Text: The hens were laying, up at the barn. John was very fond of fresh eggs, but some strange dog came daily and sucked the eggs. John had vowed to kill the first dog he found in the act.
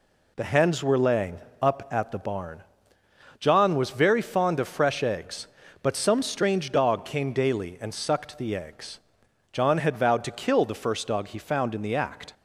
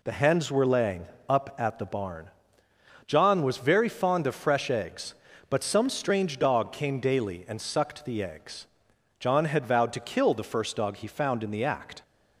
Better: neither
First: none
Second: none

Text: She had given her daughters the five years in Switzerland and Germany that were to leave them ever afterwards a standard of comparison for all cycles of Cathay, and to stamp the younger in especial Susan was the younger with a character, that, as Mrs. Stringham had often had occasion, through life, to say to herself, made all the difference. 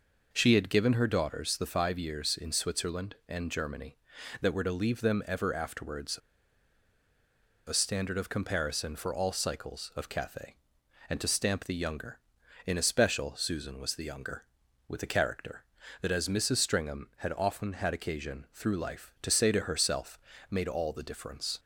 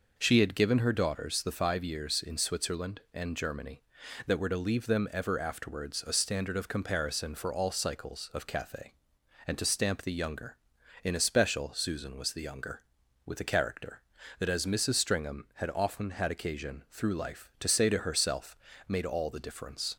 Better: second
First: pauses between "afterwards" and "a"; strong; at 6.1 s; 1.4 s long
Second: none

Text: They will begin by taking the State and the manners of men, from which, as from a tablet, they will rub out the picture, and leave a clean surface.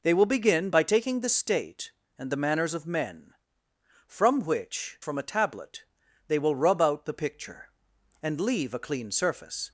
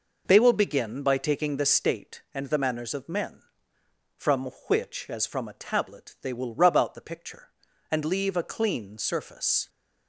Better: second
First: skips "as"; at 5.0 s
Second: none

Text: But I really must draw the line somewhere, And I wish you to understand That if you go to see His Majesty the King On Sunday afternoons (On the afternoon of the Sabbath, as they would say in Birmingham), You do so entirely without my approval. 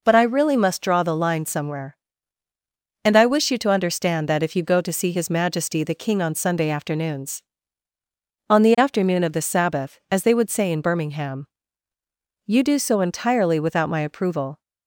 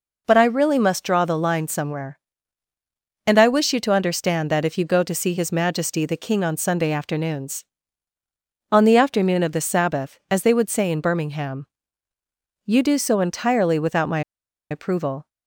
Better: first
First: none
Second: pauses between "my" and "approval"; noticeable; at 14.2 s; 0.50 s long

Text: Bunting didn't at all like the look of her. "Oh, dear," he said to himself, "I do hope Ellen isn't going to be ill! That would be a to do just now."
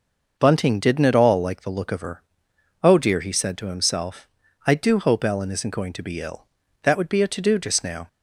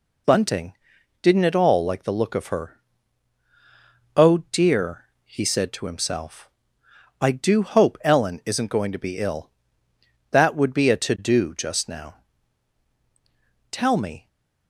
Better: first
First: none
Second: pauses between "Bunting" and "didn't"; noticeable; at 0.7 s; 0.48 s long // goes on to say "Tell me"; from 13.6 s on; 0.58 s long // stays silent after the last word; slight; from 14.1 s on; 0.5 s long

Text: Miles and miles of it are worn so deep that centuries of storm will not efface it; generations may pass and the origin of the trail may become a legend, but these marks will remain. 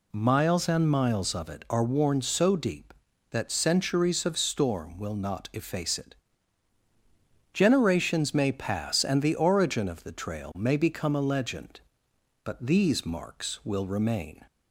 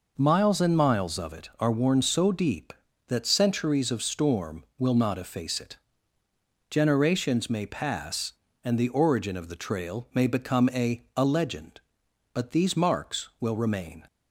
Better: first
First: none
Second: says "a" twice; at 11.1 s

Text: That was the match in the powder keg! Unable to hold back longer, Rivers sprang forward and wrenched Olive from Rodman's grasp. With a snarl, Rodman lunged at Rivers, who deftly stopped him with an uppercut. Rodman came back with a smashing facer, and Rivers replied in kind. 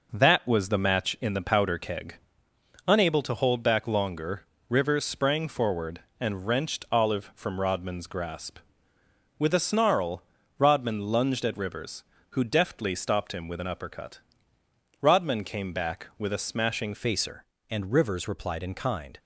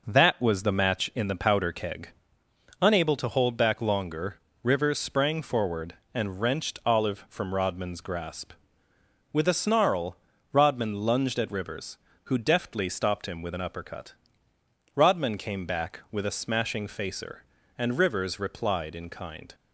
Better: second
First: changes voice at "facer"; from 16.9 s on; 2.2 s long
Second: none

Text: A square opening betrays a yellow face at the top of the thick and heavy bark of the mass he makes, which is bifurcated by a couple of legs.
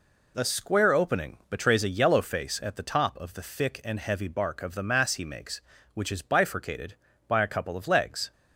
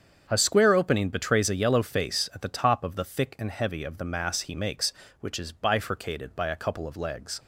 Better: first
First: none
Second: starts louder than the rest; strong; until 1.2 s; 7.5 dB // skips "bark"; at 3.8 s

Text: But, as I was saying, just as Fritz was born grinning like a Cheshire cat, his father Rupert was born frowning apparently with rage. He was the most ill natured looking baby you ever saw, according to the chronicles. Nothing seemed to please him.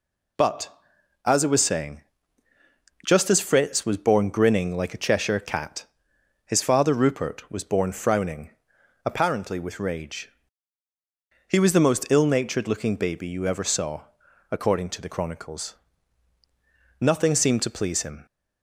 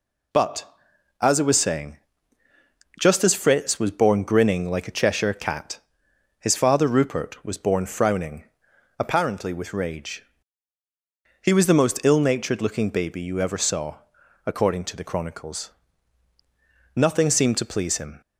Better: neither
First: pauses between "frowning" and "apparently"; noticeable; at 8.4 s; 0.56 s long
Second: pauses between "frowning" and "apparently"; noticeable; at 8.4 s; 0.56 s long

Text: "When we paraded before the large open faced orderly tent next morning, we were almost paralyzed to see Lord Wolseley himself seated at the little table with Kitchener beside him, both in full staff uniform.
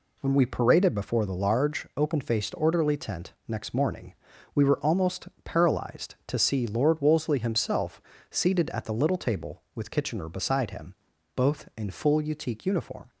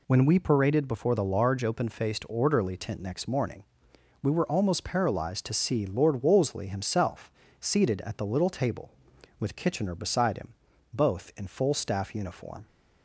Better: second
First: pauses between "almost" and "paralyzed"; slight; at 5.2 s; 0.16 s long // pauses between "himself" and "seated"; slight; at 8.0 s; 0.26 s long // says "utique" for "staff"; at 12.1 s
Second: pauses between "himself" and "seated"; slight; at 7.3 s; 0.30 s long

